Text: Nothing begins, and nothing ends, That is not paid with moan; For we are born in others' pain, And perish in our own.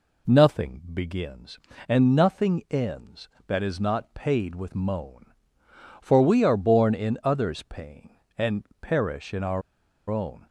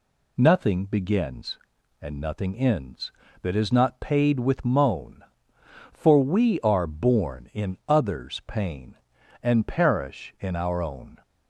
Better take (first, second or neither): second